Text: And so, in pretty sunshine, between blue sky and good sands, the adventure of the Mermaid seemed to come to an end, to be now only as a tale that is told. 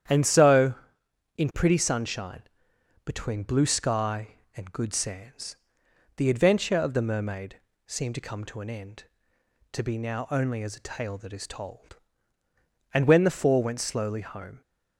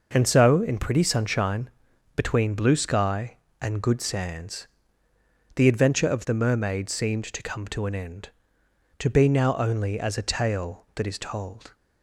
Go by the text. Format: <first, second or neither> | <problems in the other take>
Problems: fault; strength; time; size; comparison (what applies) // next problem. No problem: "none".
second | starts louder than the rest; strong; until 1.7 s; 9.5 dB // pauses between "Mermaid" and "seemed"; slight; at 7.5 s; 0.28 s long // goes on to say "And when the four went slowly home"; strong; from 12.9 s on; 1.7 s long